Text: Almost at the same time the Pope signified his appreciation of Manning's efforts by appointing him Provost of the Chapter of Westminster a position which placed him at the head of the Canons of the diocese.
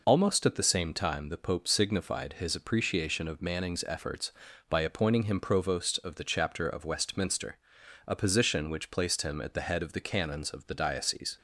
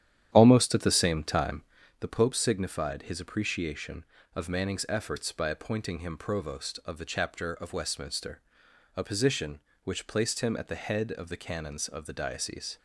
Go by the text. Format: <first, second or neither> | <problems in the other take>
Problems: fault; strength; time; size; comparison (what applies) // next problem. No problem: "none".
first | starts louder than the rest; strong; until 2.0 s; 10.5 dB // pauses between "time" and "the"; at 1.6 s; 0.38 s long // pauses between "Westminster" and "a"; noticeable; at 8.3 s; 0.56 s long; noticeable in the first